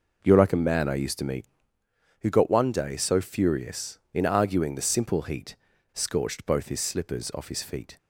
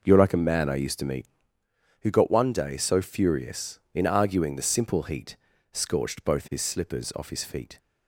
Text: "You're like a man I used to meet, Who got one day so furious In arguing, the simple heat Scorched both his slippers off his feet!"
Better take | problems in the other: neither | pauses between "heat" and "Scorched"; the same in both

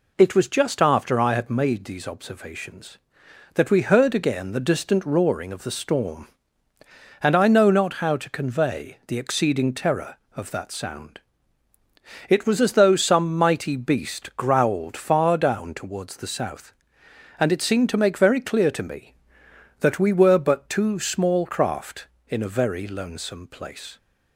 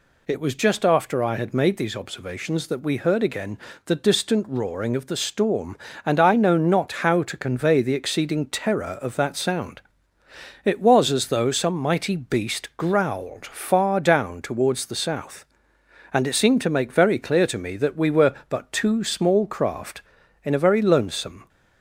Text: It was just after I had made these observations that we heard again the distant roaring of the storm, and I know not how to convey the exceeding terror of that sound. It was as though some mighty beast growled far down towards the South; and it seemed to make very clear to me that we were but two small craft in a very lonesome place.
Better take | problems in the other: first | pauses between "again" and "the"; slight; at 3.5 s; 0.26 s long // stops before "place"; at 21.4 s

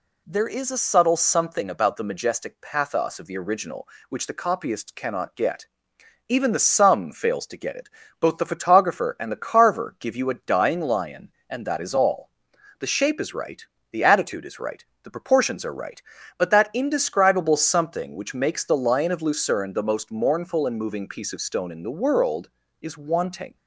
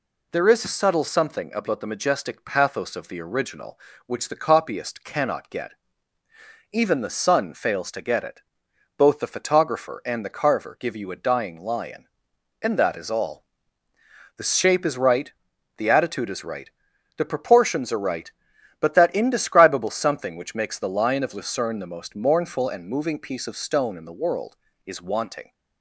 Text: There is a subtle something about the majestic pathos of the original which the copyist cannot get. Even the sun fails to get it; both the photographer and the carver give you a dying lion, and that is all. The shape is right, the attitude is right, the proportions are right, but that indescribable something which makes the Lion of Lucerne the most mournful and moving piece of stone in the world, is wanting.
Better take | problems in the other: second | says "sum" for "sun"; at 6.5 s

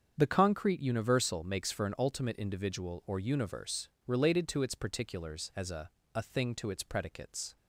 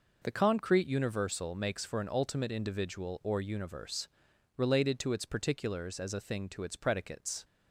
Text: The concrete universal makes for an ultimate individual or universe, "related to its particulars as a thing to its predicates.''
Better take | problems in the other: second | starts louder than the rest; strong; until 1.1 s; 7.5 dB // says "a" twice; at 6.1 s

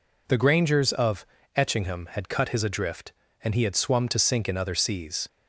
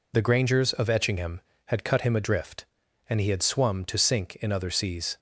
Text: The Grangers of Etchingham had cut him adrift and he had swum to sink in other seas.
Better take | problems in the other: second | pauses between "of" and "Etchingham"; slight; at 1.2 s; 0.30 s long // says "his" for "him"; at 2.4 s

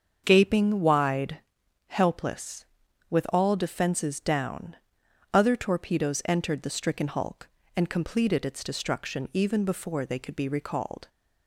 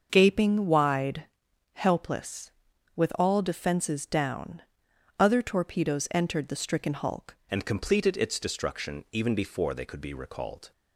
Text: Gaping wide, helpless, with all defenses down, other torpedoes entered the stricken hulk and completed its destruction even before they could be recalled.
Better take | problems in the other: first | starts louder than the rest; until 1.1 s; 6.5 dB; also in the first // changes voice at "and"; from 7.4 s on; 3.3 s long

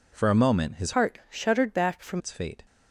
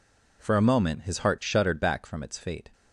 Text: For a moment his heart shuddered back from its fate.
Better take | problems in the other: second | changes voice from "heart" to "from"; from 0.9 to 2.2 s; 1.3 s long

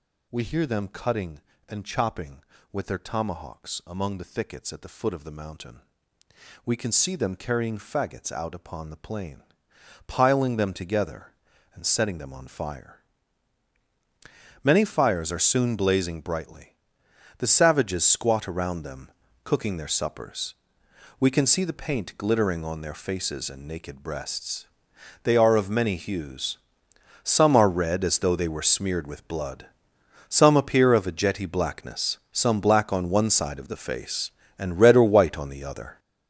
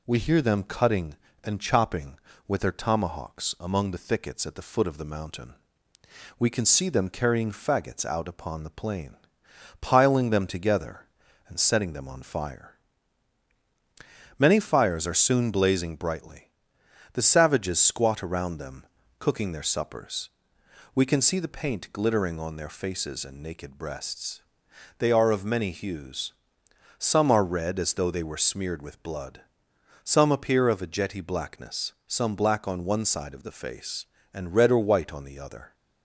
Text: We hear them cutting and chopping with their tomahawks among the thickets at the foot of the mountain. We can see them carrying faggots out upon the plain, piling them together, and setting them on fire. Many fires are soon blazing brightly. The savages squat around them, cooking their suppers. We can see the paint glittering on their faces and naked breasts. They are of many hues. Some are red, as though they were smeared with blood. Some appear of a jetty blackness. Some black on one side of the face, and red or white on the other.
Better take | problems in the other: second | gets louder; strong; throughout; 9.5 dB

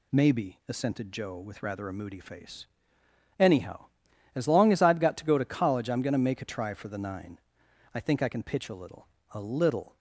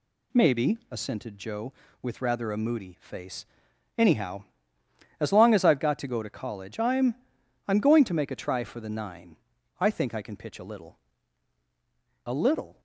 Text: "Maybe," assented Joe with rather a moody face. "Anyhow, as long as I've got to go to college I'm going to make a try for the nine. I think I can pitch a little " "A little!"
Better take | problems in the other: first | says "I'm" twice; at 7.6 s

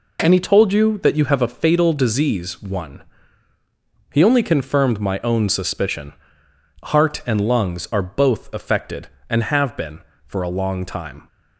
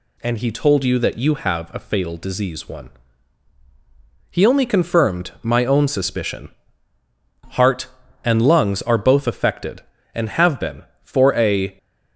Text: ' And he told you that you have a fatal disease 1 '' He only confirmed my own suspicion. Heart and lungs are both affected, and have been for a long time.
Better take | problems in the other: first | stops before "long time"; at 11.7 s

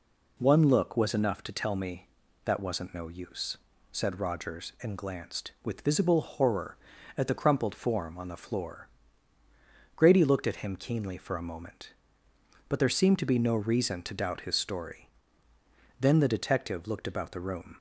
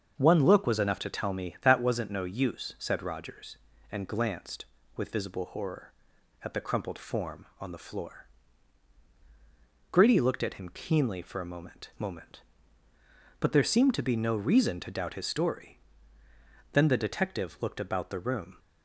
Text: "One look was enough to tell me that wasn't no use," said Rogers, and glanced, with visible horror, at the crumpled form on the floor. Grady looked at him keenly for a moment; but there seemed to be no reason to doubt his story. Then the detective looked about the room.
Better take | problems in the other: first | starts louder than the rest; until 1.1 s; 6.5 dB // says "moment" twice; at 11.9 s

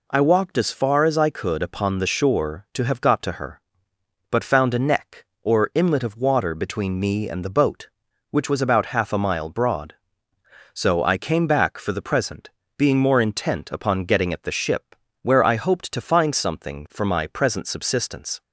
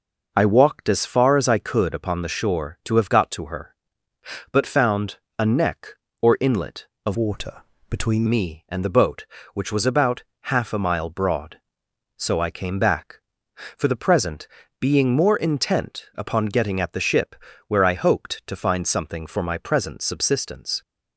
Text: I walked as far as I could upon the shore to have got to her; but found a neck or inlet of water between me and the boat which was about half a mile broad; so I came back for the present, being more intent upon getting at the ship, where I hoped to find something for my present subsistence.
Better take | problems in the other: first | pauses between "found" and "a"; slight; at 5.1 s; 0.22 s long // changes voice from "water" to "between"; from 7.1 to 8.2 s; 1.1 s long // pauses between "water" and "between"; slight; at 7.6 s; 0.26 s long // pauses between "about" and "half"; slight; at 10.2 s; 0.22 s long

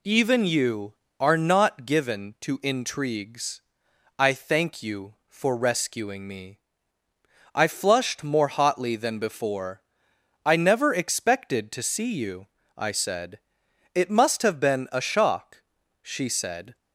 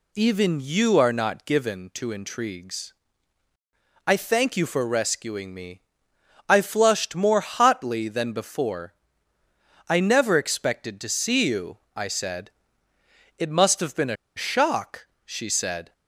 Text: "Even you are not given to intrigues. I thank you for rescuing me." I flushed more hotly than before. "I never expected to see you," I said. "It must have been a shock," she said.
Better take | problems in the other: first | pauses between "a" and "shock"; slight; at 14.1 s; 0.22 s long

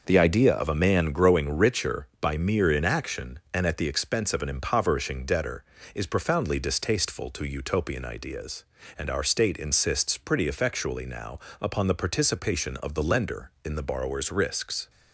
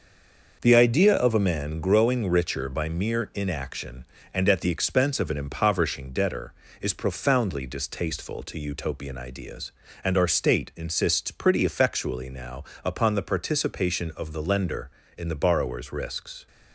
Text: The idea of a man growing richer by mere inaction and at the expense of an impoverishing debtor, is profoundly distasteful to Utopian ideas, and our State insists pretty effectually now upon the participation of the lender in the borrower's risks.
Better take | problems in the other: first | stays silent before the first word; slight; until 0.6 s; 0.6 s long // starts louder than the rest; noticeable; until 1.6 s; 6 dB // pauses between "now" and "upon"; slight; at 12.6 s; 0.18 s long; slight in the first

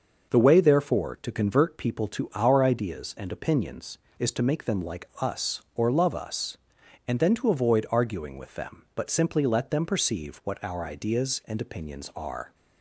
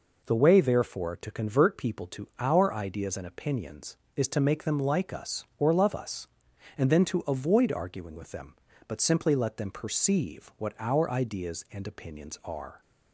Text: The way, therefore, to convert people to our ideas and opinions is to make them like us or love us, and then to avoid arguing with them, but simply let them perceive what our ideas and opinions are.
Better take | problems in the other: neither | none

